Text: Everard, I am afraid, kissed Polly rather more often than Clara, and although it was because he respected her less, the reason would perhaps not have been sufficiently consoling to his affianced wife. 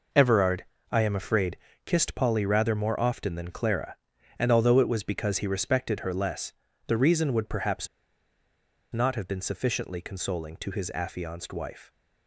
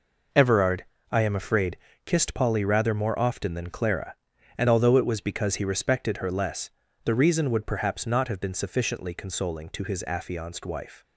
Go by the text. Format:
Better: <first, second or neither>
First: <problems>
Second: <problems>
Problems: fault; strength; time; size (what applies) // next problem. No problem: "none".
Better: second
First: pauses between "perhaps" and "not"; at 7.8 s; 1.0 s long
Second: none